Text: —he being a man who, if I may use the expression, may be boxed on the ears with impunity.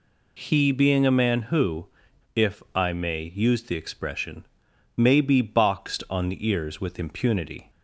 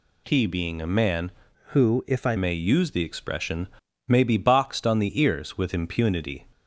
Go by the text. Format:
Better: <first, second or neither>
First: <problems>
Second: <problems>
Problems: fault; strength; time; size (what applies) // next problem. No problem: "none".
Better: first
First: none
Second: changes voice from "who" to "I"; from 1.6 to 2.3 s; 0.7 s long